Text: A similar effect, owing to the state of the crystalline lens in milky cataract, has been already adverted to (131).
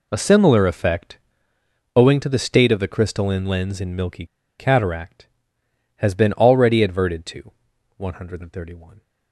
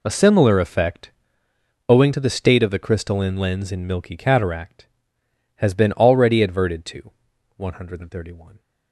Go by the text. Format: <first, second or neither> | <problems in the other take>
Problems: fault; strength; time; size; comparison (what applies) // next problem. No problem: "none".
second | pauses between "milky" and "cataract"; slight; at 4.2 s; 0.34 s long